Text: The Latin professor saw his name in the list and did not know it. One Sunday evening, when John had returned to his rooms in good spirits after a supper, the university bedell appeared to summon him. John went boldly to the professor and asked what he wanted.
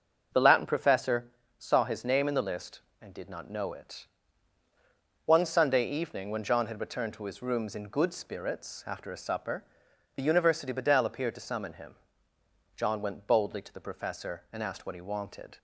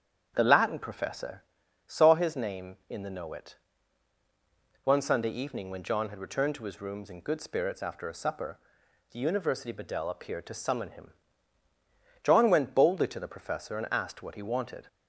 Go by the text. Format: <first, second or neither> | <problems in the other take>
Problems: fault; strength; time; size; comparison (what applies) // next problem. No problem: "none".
first | starts louder than the rest; strong; until 1.3 s; 8.5 dB; also in the first // pauses between "professor" and "saw"; at 1.4 s; 0.42 s long; slight in the first // skips "list and did not"; at 3.0 s